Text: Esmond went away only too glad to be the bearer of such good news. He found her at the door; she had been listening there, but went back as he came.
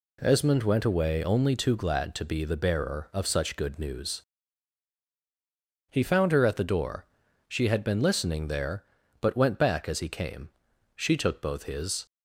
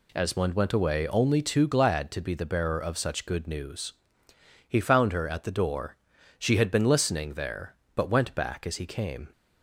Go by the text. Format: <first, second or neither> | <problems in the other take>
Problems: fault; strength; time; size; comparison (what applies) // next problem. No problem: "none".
second | goes on to say "She took both his"; noticeable; from 10.9 s on; 1.1 s long